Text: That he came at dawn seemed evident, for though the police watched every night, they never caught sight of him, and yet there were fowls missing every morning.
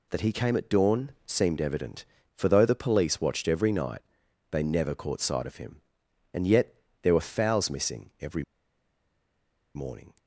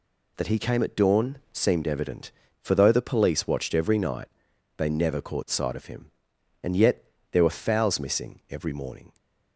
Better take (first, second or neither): second